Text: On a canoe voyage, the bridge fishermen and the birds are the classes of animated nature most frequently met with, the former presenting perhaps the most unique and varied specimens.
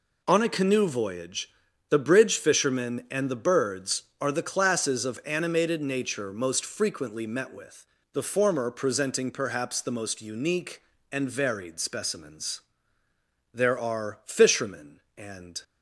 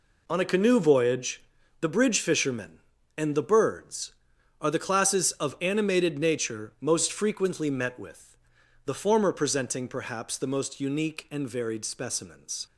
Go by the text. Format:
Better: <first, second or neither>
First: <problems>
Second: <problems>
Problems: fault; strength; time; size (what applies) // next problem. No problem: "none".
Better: second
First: goes on to say "There are fishermen and"; strong; from 13.5 s on; 2.1 s long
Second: none